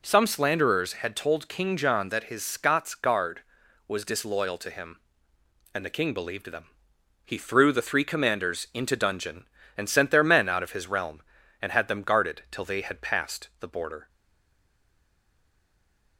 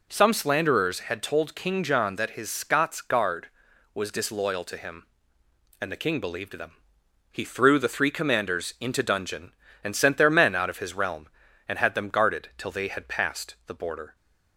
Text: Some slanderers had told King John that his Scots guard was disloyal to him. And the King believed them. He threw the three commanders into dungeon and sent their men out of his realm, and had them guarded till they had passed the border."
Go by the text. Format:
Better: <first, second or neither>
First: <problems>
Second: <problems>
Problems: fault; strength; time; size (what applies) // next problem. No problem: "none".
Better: second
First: stays silent after the last word; from 14.0 s on; 2.1 s long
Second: none